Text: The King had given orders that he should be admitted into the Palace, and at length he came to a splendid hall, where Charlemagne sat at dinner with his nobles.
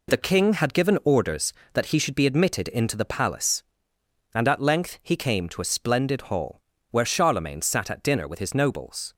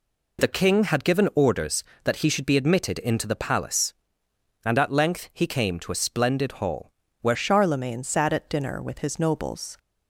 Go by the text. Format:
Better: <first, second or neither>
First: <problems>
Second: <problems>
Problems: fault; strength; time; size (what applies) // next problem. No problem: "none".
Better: first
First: none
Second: changes voice at "Charlemagne"; from 7.3 s on; 2.4 s long